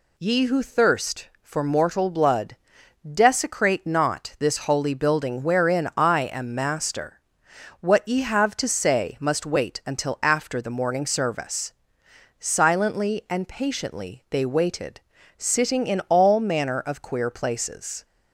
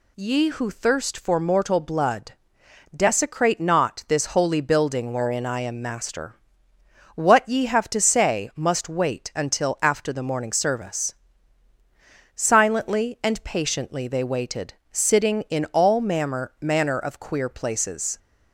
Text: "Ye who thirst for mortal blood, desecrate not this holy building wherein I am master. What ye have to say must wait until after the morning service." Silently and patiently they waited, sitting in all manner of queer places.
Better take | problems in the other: first | says "manner" twice; at 16.5 s

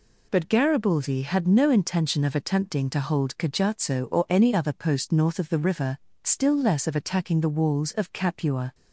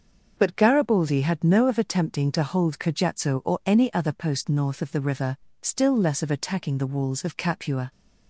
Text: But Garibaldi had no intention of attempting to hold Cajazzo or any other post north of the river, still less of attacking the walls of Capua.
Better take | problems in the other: first | starts louder than the rest; until 1.3 s; 6.5 dB // skips "intention"; at 1.6 s

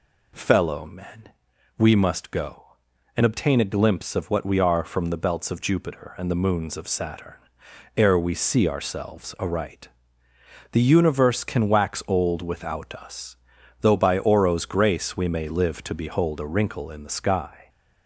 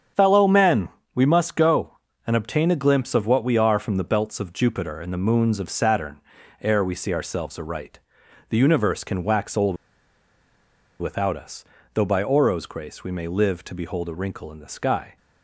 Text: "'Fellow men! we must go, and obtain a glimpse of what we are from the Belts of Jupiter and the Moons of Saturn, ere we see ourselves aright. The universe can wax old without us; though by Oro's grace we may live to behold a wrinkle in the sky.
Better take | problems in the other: first | starts louder than the rest; strong; until 1.4 s; 8 dB // pauses between "old" and "without"; at 9.7 s; 1.2 s long

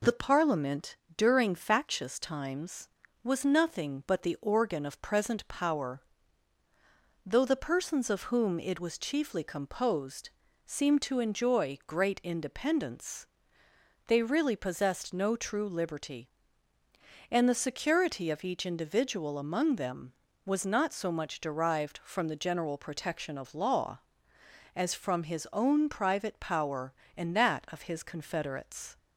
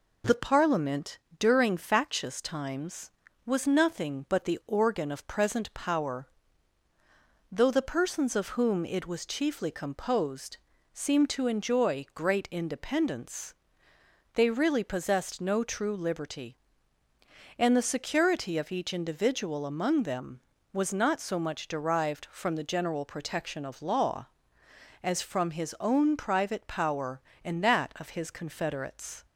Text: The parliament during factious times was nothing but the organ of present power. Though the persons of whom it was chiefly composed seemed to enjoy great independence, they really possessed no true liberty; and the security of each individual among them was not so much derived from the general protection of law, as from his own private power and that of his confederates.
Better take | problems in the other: neither | pauses between "parliament" and "during"; slight; the same in both // pauses between "composed" and "seemed"; slight; the same in both

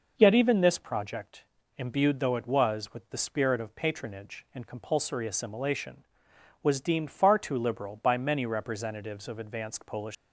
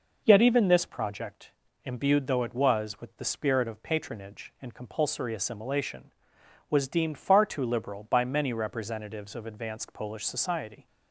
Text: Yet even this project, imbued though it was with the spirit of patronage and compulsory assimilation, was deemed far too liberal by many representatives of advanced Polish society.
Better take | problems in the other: second | stops before "society"; at 10.1 s

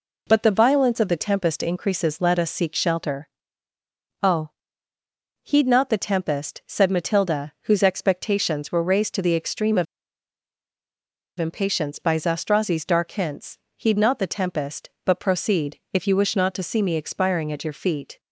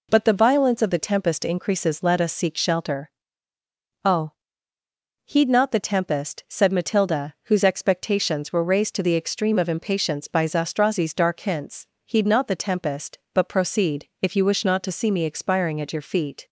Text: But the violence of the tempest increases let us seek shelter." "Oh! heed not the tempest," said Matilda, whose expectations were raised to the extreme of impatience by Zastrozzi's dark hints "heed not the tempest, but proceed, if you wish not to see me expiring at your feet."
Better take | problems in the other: second | pauses between "of" and "impatience"; strong; at 9.8 s; 1.5 s long // pauses between "hints" and "heed"; slight; at 13.5 s; 0.20 s long; slight in the second

